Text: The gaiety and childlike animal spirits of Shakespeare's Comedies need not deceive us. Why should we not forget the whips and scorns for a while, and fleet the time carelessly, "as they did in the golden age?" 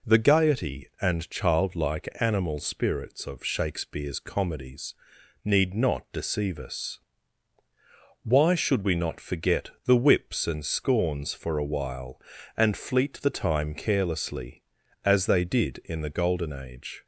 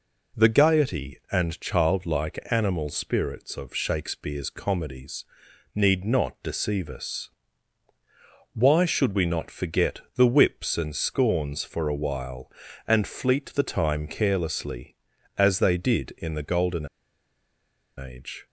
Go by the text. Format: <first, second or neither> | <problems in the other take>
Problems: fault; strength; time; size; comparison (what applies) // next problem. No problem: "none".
first | pauses between "Comedies" and "need"; noticeable; at 5.2 s; 0.52 s long; noticeable in the first // pauses between "forget" and "the"; slight; at 10.0 s; 0.16 s long; slight in the first // pauses between "golden" and "age"; at 16.8 s; 1.1 s long